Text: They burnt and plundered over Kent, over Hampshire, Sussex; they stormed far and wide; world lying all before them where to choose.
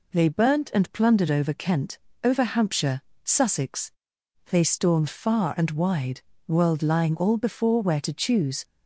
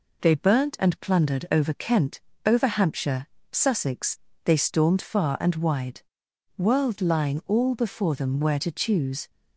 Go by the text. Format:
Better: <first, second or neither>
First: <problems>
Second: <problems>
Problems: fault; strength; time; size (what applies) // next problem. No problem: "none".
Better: second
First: skips "them"; at 7.8 s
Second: none